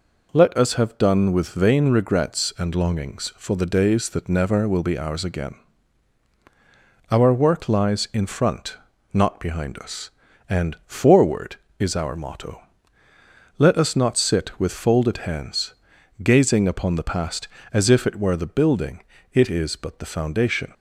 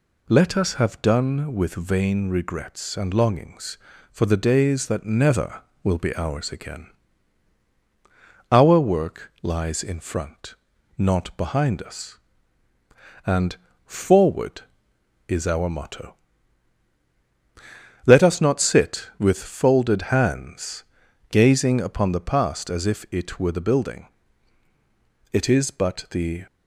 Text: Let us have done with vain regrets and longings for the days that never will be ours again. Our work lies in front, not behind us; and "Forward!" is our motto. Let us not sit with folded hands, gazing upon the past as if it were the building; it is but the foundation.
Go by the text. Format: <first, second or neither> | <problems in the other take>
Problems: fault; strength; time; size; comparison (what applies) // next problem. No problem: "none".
first | pauses between "and" and "Forward"; slight; at 13.5 s; 0.30 s long // stops before "foundation"; at 26.4 s